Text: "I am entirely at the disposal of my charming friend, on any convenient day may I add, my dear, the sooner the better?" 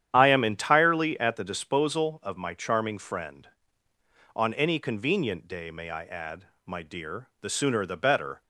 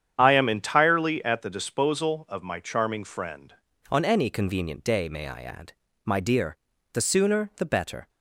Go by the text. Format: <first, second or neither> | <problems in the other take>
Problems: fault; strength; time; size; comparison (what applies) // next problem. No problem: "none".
first | starts louder than the rest; strong; until 1.1 s; 9 dB; strong in the first // changes voice at "on"; from 3.8 s on; 4.2 s long